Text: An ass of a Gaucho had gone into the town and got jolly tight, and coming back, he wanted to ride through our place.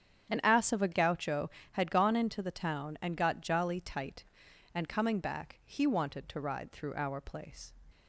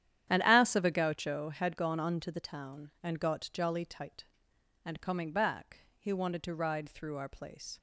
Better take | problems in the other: first | starts louder than the rest; strong; until 1.3 s; 10.5 dB; strong in the first // says "unto" for "into"; at 1.9 s

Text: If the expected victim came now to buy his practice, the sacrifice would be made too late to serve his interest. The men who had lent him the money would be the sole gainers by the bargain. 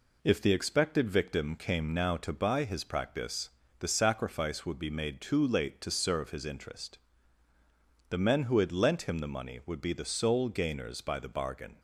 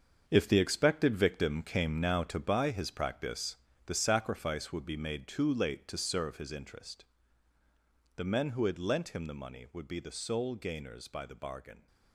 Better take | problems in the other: first | gets quieter; strong; throughout; 10.5 dB

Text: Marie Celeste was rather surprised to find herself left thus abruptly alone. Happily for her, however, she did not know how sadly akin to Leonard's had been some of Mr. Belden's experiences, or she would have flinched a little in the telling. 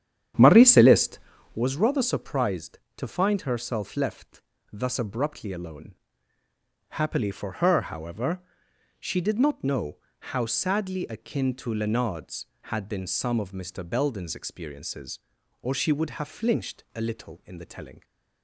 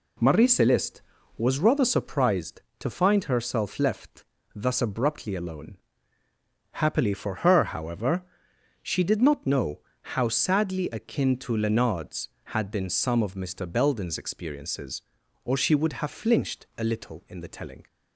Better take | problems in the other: second | starts louder than the rest; strong; until 1.6 s; 9.5 dB // pauses between "left" and "thus"; slight; at 4.4 s; 0.28 s long; slight in the second // pauses between "know" and "how"; slight; at 9.9 s; 0.24 s long; slight in the second

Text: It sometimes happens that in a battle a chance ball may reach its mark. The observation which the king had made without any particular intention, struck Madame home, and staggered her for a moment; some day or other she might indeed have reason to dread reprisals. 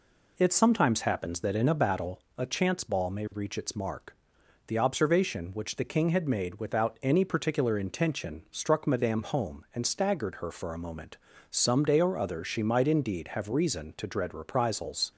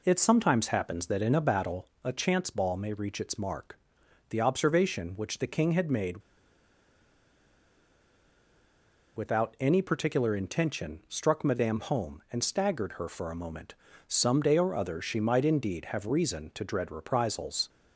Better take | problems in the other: first | pauses between "battle" and "a"; slight; at 1.8 s; 0.16 s long; slight in the first // pauses between "made" and "without"; strong; at 6.2 s; 2.9 s long

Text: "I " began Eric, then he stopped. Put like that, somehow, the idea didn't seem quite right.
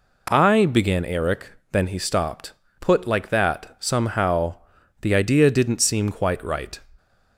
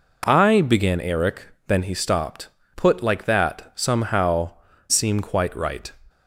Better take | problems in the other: first | skips "the idea didn't"; at 4.7 s

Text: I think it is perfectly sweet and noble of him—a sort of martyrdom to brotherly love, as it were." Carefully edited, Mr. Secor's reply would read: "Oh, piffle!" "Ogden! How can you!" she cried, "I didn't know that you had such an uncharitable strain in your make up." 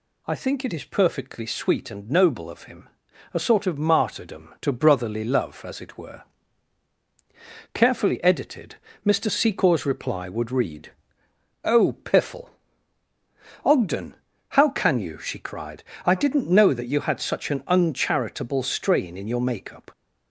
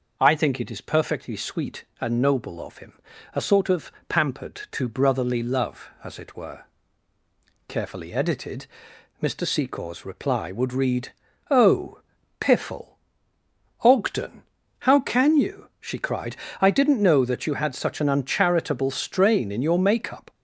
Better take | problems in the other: first | says "pampered" for "martyrdom"; at 4.0 s

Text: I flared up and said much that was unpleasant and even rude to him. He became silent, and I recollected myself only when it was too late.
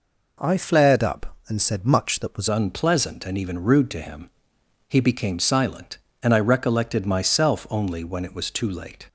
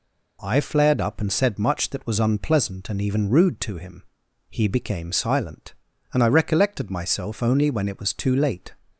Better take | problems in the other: second | changes voice at "unpleasant"; from 2.4 s on; 6.6 s long

